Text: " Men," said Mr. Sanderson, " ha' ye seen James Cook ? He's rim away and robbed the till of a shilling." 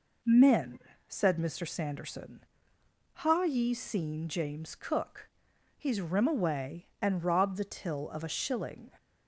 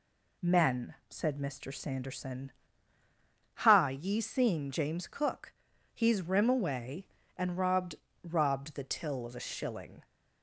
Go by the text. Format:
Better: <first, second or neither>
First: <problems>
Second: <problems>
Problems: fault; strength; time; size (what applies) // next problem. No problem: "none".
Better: first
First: none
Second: says "robbed" twice; at 8.2 s